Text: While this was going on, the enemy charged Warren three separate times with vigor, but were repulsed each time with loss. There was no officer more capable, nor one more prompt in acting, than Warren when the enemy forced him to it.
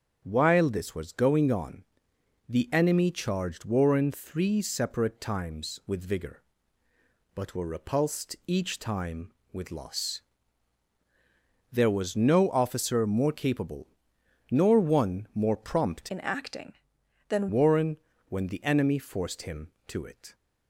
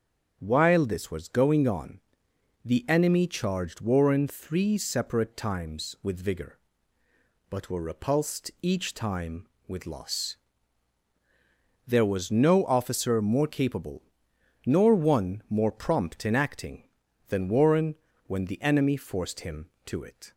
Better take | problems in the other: second | starts louder than the rest; strong; until 1.2 s; 7.5 dB; strong in the second // changes voice from "in" to "than"; from 16.0 to 17.4 s; 1.4 s long // pauses between "Warren" and "when"; slight; at 17.9 s; 0.32 s long; slight in the second

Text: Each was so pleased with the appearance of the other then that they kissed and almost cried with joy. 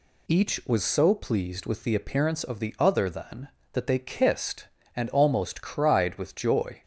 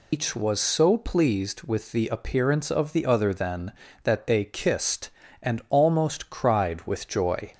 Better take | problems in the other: first | loses the start of "Each"; at 0.1 s; 140 ms

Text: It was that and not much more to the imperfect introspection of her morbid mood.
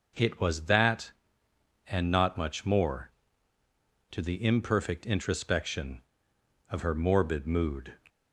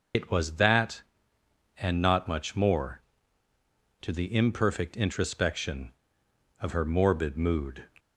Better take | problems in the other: first | loses the start of "It"; at 0.1 s; 90 ms

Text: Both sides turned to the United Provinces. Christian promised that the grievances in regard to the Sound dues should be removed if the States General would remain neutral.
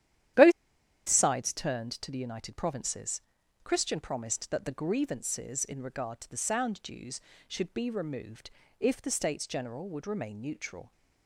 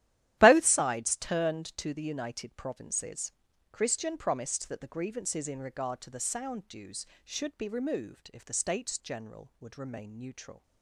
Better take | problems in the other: second | starts louder than the rest; strong; until 1.9 s; 11.5 dB; strong in the second // pauses between "Both" and "sides"; noticeable; at 0.5 s; 0.56 s long // pauses between "removed" and "if"; slight; at 8.4 s; 0.30 s long

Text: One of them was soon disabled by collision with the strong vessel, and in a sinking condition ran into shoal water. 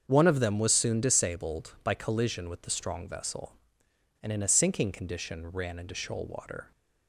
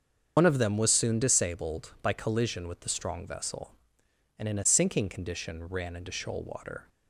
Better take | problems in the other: first | loses the start of "One"; at 0.3 s; 100 ms // starts louder than the rest; until 1.3 s; 7 dB; also in the first

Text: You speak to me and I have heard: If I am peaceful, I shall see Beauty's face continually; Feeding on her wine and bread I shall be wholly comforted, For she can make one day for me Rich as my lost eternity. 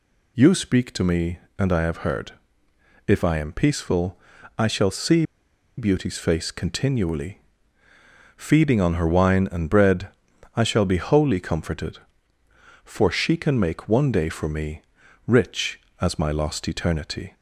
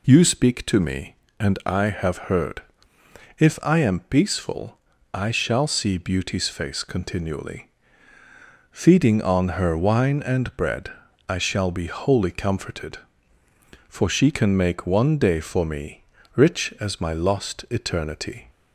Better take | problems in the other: second | pauses between "see" and "Beauty's"; noticeable; at 5.2 s; 0.54 s long // pauses between "bread" and "I"; noticeable; at 10.0 s; 0.48 s long; also in the second // pauses between "me" and "Rich"; noticeable; at 14.8 s; 0.46 s long; slight in the second

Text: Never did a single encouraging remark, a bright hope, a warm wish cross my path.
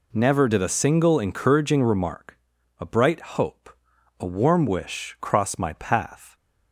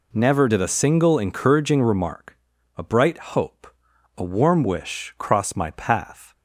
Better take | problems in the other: neither | pauses between "bright" and "hope"; slight; the same in both

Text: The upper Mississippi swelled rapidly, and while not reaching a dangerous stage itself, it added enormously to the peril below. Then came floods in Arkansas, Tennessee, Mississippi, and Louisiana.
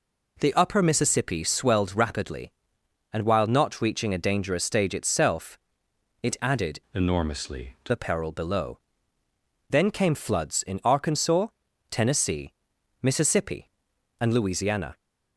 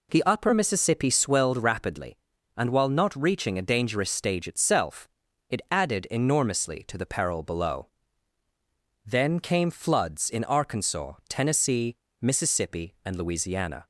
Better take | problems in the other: second | changes voice from "enormously" to "to"; from 6.9 to 7.9 s; 1.0 s long

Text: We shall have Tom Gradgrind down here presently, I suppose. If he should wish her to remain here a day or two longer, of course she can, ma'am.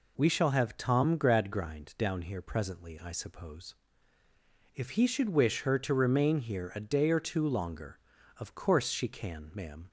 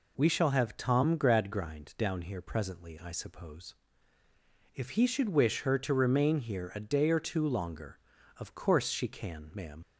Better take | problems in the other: first | leaves "ma'am" unfinished; at 9.8 s; 65 ms

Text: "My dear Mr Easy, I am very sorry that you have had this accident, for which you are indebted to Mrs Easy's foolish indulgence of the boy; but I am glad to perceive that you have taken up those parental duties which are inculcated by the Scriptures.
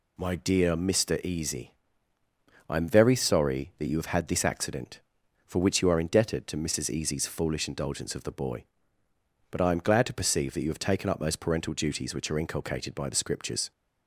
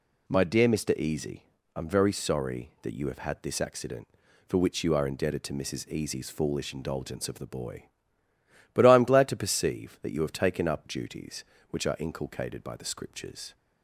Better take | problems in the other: first | skips "those parental"; at 10.8 s

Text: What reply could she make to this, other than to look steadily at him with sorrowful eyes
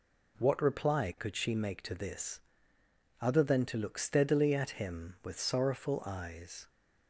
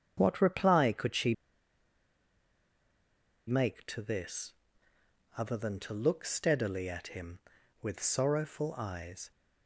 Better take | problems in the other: first | starts louder than the rest; strong; until 1.1 s; 7.5 dB // pauses between "she" and "make"; strong; at 1.3 s; 2.1 s long

